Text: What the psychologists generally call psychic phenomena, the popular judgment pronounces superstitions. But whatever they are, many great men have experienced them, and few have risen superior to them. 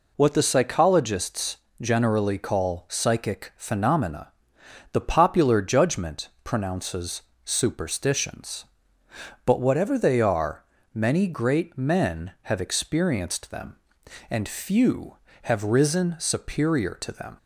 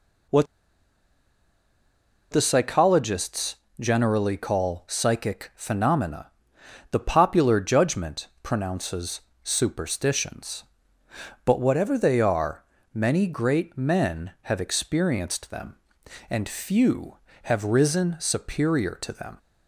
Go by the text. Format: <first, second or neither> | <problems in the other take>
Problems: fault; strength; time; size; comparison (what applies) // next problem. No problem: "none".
first | pauses between "What" and "the"; strong; at 0.4 s; 1.8 s long // pauses between "psychologists" and "generally"; slight; at 3.5 s; 0.24 s long; slight in the first // pauses between "judgment" and "pronounces"; slight; at 8.2 s; 0.16 s long; slight in the first // pauses between "pronounces" and "superstitions"; slight; at 9.2 s; 0.24 s long; slight in the first